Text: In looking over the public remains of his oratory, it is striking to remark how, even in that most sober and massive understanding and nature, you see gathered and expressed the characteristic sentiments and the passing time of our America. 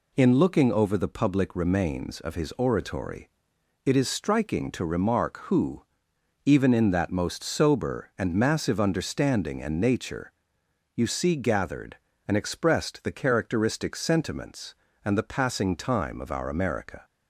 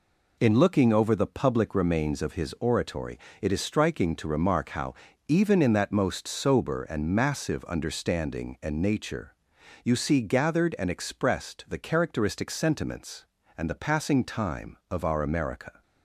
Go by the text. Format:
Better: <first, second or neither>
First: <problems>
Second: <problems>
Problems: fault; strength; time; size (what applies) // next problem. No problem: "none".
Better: second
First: says "who" for "how"; at 5.4 s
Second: none